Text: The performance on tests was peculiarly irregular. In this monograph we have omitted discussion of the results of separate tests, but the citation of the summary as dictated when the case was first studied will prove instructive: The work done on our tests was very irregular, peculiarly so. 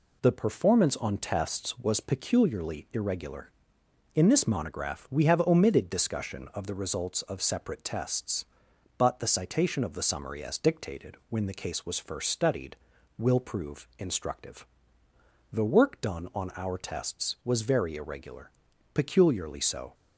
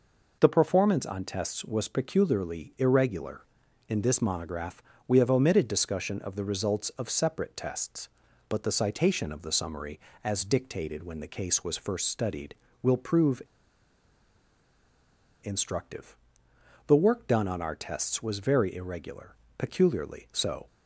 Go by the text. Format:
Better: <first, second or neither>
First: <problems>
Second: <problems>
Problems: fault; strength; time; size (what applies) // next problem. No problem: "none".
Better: first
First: none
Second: pauses between "monograph" and "we"; slight; at 4.8 s; 0.28 s long // pauses between "prove" and "instructive"; strong; at 13.4 s; 2.0 s long